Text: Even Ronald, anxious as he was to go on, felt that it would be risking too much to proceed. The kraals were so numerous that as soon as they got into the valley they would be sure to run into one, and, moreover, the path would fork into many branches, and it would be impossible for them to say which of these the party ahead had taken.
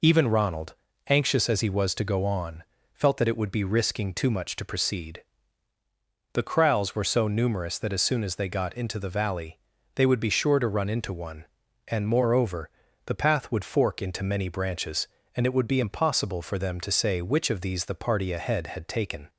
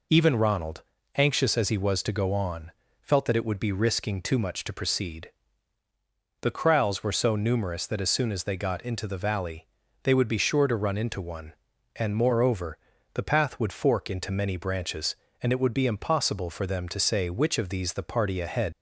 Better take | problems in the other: first | pauses between "valley" and "they"; slight; at 9.6 s; 0.36 s long; slight in the first // stops before "had taken"; at 18.7 s

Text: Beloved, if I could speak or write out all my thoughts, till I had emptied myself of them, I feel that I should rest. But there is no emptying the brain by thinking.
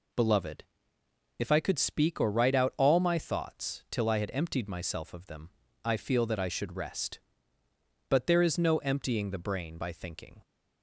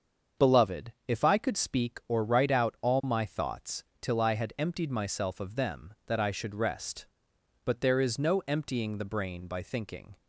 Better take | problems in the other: first | starts louder than the rest; until 1.5 s; 7 dB // skips "I feel"; at 6.0 s

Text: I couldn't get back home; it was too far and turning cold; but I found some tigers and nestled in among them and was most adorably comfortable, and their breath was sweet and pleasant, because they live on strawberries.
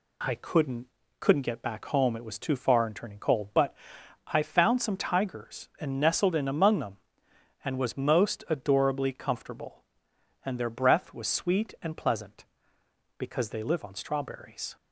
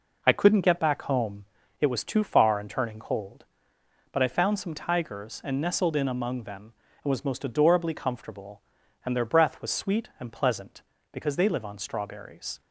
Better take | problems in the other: second | says "couldn't" twice; at 1.1 s // pauses between "but" and "I"; noticeable; at 3.7 s; 0.54 s long

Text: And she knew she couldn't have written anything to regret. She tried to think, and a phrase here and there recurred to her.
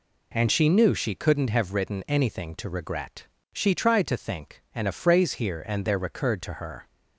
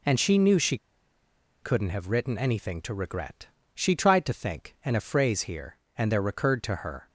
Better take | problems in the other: first | pauses between "she" and "couldn't"; noticeable; at 0.7 s; 0.86 s long

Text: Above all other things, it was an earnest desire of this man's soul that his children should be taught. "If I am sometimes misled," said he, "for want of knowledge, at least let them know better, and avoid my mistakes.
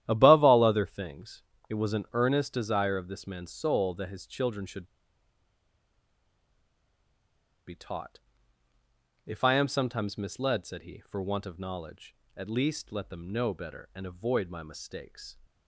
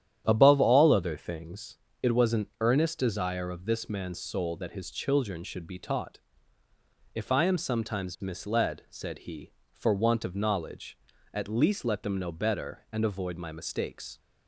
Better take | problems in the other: second | starts louder than the rest; strong; until 1.0 s; 12 dB; strong in the second // pauses between "should" and "be"; strong; at 4.8 s; 2.8 s long

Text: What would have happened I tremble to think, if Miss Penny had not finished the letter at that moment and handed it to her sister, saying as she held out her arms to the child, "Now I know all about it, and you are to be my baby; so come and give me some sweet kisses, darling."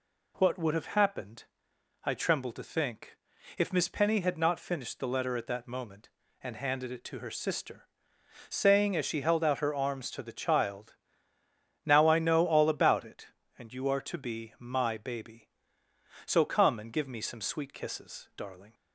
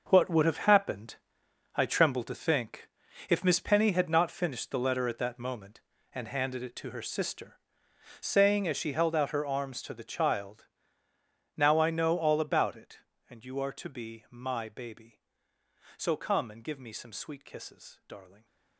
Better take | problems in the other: first | gets quieter; strong; throughout; 12 dB // pauses between "happened" and "I"; noticeable; at 1.1 s; 0.60 s long; noticeable in the first

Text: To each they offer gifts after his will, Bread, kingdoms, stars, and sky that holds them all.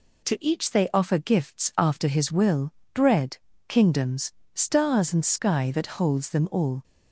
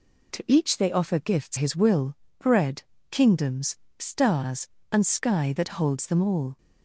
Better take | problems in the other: first | skips "after"; at 1.5 s

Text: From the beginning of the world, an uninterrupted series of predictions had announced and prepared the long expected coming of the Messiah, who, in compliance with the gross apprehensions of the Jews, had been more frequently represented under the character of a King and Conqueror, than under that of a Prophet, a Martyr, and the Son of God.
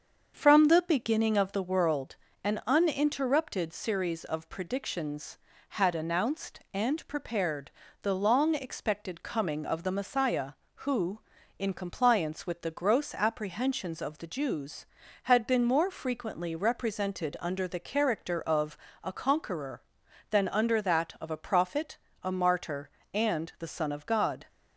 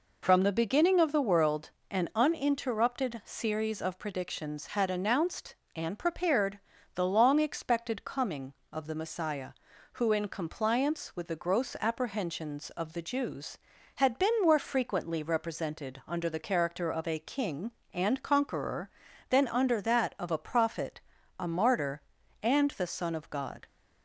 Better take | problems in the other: second | starts louder than the rest; until 1.3 s; 7 dB // pauses between "prepared" and "the"; slight; at 7.7 s; 0.30 s long; slight in the second // pauses between "of" and "a"; slight; at 18.7 s; 0.28 s long // skips "King and"; at 19.1 s

